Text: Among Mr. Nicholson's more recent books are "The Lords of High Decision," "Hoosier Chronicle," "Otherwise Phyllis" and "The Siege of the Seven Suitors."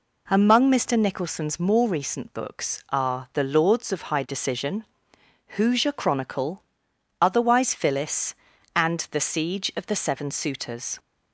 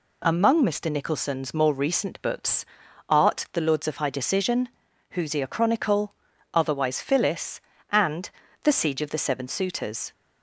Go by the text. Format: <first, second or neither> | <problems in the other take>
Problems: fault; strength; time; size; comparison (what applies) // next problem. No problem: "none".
first | says "art" for "are"; at 3.0 s // pauses between "and" and "The"; slight; at 8.2 s; 0.32 s long